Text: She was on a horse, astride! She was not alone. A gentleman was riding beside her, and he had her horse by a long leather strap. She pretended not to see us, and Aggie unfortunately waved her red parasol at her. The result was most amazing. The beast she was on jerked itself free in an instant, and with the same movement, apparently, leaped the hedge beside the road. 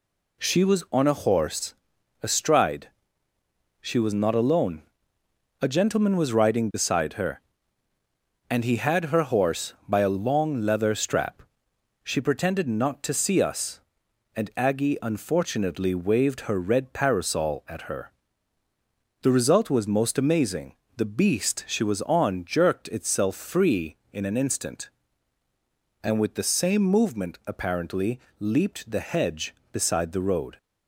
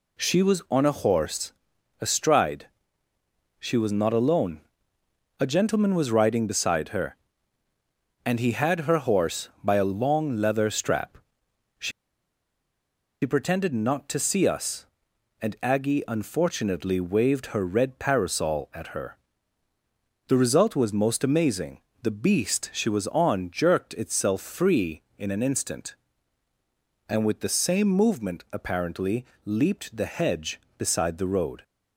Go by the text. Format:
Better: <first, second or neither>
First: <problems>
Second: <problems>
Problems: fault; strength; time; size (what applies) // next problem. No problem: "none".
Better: first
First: none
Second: pauses between "She" and "pretended"; strong; at 11.9 s; 1.3 s long